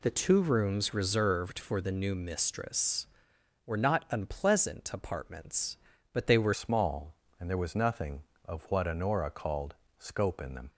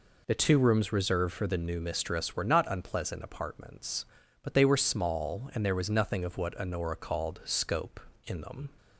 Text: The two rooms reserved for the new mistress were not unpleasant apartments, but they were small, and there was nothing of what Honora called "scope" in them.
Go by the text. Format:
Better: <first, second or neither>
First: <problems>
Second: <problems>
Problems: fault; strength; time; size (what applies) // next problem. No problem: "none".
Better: second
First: changes voice at "small"; from 6.5 s on; 4.1 s long // pauses between "called" and "scope"; slight; at 9.7 s; 0.24 s long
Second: none